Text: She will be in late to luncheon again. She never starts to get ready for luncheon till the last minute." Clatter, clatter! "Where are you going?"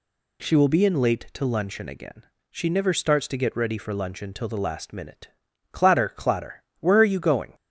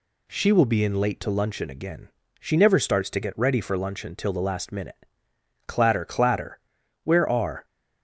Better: first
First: none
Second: stops before "you going"; at 7.6 s

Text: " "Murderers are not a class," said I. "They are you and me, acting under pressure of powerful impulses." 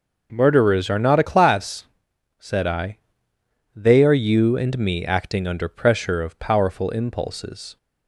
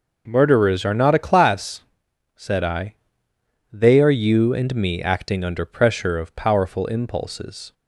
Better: neither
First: none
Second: none

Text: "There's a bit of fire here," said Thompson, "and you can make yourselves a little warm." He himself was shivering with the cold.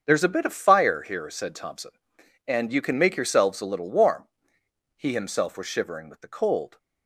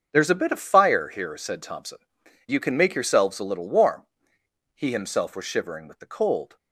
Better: first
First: starts louder than the rest; until 1.0 s; 7 dB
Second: starts louder than the rest; until 1.1 s; 6.5 dB // skips "and"; at 2.2 s

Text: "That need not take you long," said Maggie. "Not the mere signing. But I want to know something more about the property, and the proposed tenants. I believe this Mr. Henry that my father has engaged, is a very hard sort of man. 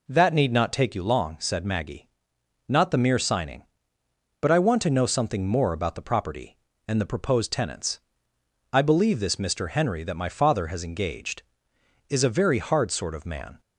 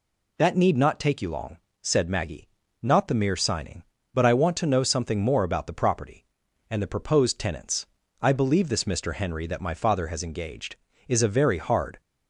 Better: first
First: none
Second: stops before "sort of man"; at 12.0 s

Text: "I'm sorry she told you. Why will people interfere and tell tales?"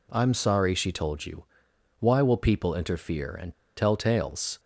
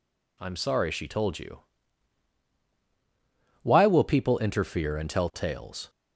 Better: second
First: pauses between "and" and "tell"; slight; at 3.5 s; 0.23 s long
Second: none

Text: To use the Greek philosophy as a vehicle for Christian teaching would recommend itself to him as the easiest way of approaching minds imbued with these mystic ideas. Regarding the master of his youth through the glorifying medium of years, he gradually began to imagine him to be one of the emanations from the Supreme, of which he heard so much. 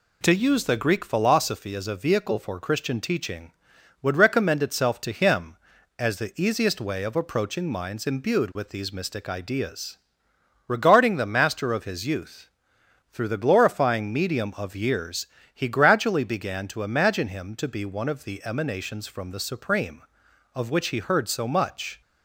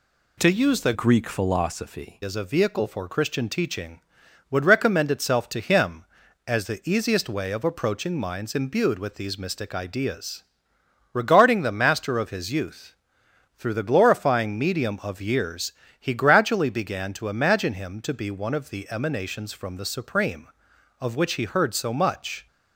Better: first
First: pauses between "youth" and "through"; noticeable; at 12.4 s; 0.62 s long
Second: changes voice from "Greek" to "philosophy"; from 0.9 to 2.2 s; 1.3 s long // pauses between "youth" and "through"; noticeable; at 12.9 s; 0.62 s long

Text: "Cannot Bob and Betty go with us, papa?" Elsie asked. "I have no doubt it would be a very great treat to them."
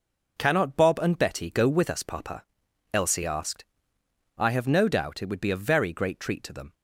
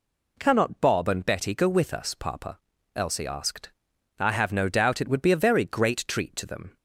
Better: neither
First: none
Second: none

